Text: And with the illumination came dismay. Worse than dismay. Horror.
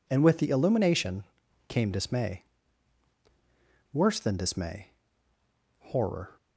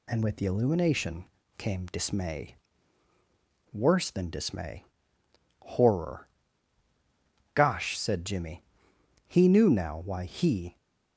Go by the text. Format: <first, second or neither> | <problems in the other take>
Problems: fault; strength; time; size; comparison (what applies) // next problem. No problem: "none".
first | pauses between "illumination" and "came"; slight; at 1.2 s; 0.34 s long; also in the first // goes on to say "Gosh said Jimmy He knew now why he"; strong; from 7.5 s on; 3.2 s long